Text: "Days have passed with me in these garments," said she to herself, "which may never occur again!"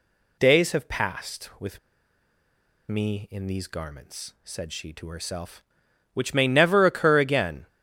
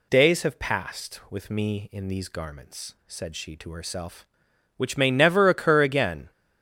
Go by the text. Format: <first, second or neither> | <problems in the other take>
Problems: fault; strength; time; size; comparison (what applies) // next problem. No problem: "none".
second | pauses between "with" and "me"; at 1.7 s; 1.1 s long